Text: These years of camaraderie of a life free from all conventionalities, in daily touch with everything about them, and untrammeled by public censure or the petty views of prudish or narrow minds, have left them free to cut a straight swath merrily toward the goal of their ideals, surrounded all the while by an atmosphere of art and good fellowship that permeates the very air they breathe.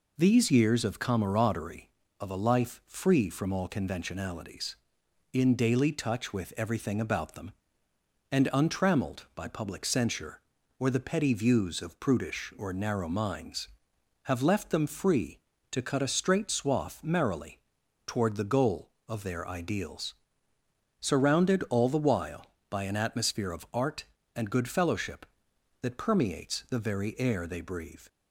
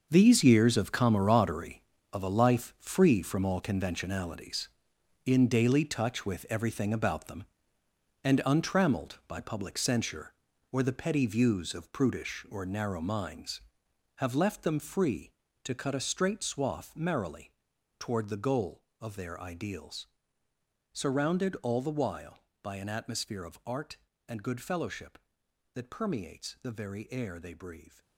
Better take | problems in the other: first | gets quieter; strong; throughout; 11.5 dB // pauses between "merrily" and "toward"; noticeable; at 17.5 s; 0.48 s long; noticeable in the first

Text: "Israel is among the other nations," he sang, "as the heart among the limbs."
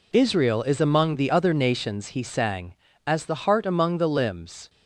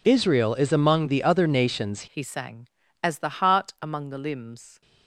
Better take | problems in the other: first | changes voice at "he"; from 2.0 s on; 2.8 s long

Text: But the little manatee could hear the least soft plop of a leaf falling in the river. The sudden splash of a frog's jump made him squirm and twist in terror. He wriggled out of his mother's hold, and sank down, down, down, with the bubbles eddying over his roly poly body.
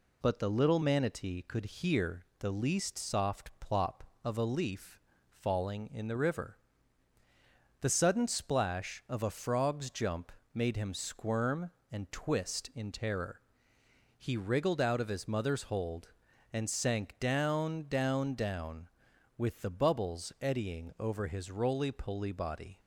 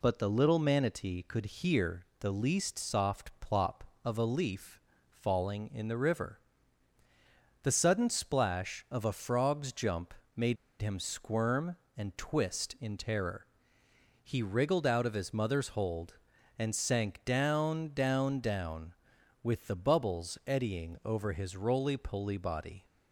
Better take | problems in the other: first | pauses between "leaf" and "falling"; slight; at 4.8 s; 0.26 s long; slight in the first // pauses between "jump" and "made"; slight; at 10.1 s; 0.20 s long; slight in the first // pauses between "made" and "him"; slight; at 10.5 s; 0.24 s long

